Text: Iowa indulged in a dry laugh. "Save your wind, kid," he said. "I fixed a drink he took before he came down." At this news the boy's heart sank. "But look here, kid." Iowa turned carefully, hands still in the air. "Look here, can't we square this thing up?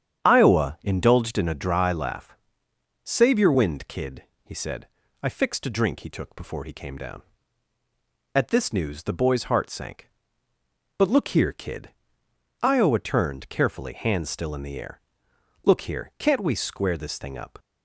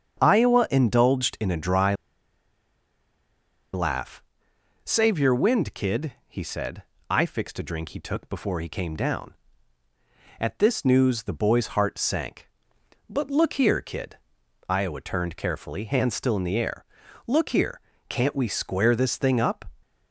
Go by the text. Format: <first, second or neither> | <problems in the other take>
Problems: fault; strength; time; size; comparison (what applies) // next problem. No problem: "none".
first | starts louder than the rest; strong; until 1.2 s; 7.5 dB; strong in the first // pauses between "dry" and "laugh"; strong; at 1.9 s; 1.7 s long